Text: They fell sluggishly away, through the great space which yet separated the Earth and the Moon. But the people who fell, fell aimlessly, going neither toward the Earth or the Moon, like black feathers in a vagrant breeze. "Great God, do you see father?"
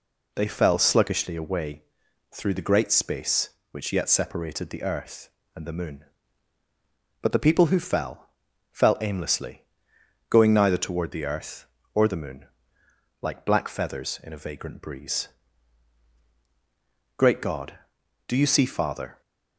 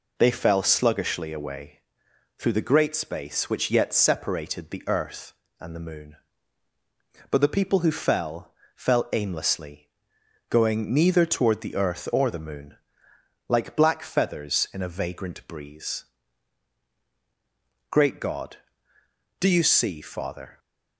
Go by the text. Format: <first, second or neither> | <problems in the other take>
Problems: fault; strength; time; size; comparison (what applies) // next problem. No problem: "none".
neither | none